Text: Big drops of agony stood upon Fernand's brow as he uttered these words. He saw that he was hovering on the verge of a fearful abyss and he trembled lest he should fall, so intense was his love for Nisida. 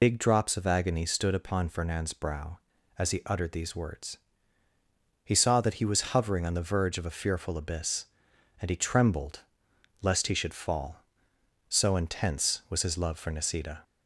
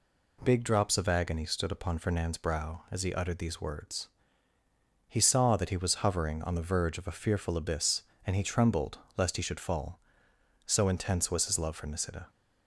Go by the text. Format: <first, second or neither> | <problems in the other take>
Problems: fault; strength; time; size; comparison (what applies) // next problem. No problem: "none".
second | loses the start of "Big"; at 0.0 s; 65 ms // pauses between "trembled" and "lest"; noticeable; at 9.4 s; 0.60 s long; slight in the second